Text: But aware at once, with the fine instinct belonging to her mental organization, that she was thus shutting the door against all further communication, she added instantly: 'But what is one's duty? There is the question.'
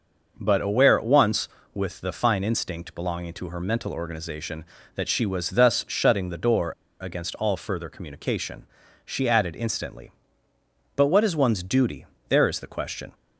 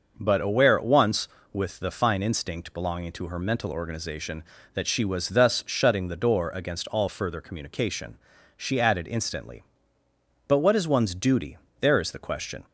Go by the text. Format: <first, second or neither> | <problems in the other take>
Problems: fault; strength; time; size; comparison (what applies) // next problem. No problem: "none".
second | starts louder than the rest; noticeable; until 1.4 s; 6 dB; noticeable in the second // pauses between "door" and "against"; slight; at 6.7 s; 0.30 s long